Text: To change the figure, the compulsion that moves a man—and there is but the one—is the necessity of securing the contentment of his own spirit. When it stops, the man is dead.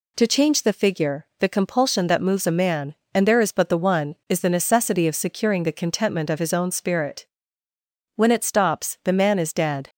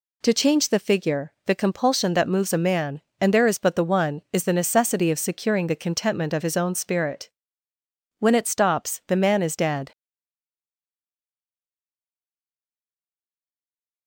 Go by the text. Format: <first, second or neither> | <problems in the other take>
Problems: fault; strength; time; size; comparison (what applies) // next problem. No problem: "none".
first | stays silent after the last word; strong; from 9.9 s on; 4.1 s long